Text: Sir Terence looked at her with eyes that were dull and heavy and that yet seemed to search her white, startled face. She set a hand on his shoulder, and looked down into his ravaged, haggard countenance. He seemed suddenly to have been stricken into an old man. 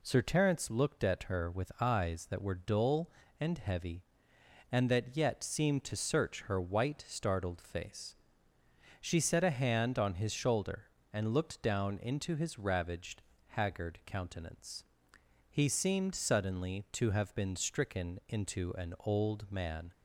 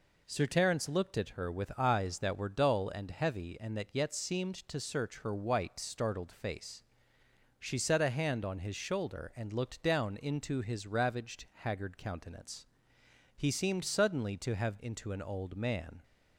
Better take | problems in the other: first | skips "been stricken"; at 14.7 s

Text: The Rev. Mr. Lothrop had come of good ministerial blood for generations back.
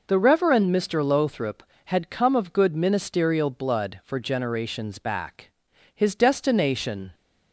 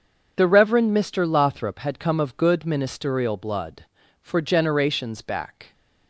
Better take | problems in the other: second | goes on to say "His destination"; noticeable; from 5.9 s on; 1.2 s long

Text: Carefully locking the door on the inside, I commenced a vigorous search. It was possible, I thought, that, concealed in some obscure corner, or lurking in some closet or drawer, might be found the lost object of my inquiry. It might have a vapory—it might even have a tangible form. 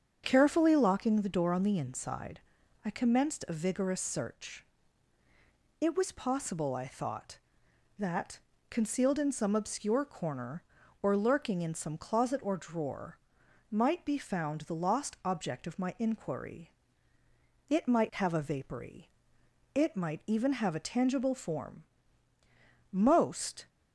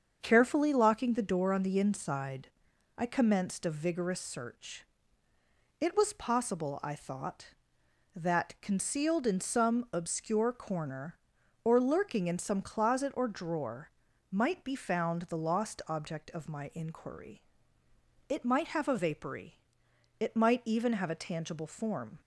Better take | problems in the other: second | starts louder than the rest; strong; until 1.2 s; 7.5 dB; also in the second // goes on to say "Most"; noticeable; from 22.9 s on; 0.76 s long

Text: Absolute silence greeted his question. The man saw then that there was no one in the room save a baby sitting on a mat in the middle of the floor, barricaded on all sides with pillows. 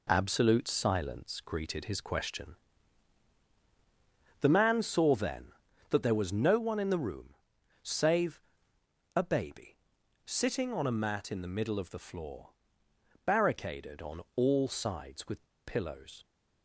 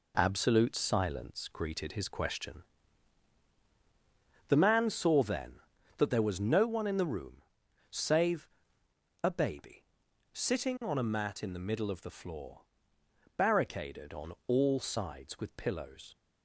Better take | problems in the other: second | pauses between "room" and "save"; noticeable; at 7.3 s; 0.48 s long; noticeable in the second // pauses between "save" and "a"; noticeable; at 8.4 s; 0.74 s long; noticeable in the second // pauses between "baby" and "sitting"; noticeable; at 9.7 s; 0.48 s long; noticeable in the second // pauses between "with" and "pillows"; slight; at 15.4 s; 0.22 s long

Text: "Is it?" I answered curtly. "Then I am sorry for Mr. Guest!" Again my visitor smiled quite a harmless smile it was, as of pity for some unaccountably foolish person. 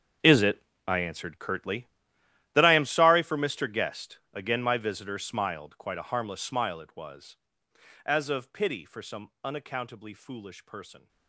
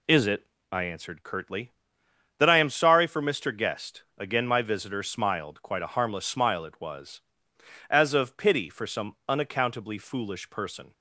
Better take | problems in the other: second | gets quieter; strong; throughout; 16.5 dB

